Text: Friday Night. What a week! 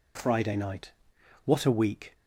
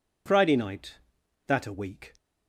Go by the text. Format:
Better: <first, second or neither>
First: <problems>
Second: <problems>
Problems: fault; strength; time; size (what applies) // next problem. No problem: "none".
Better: first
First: none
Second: says "That" for "What"; at 1.4 s